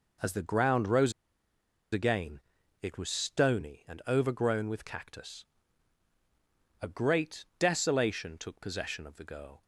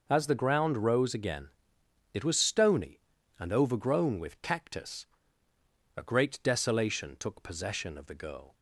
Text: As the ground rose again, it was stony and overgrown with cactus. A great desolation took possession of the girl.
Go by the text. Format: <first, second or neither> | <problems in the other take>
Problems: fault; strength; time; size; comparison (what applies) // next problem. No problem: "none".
second | pauses between "rose" and "again"; noticeable; at 1.1 s; 0.80 s long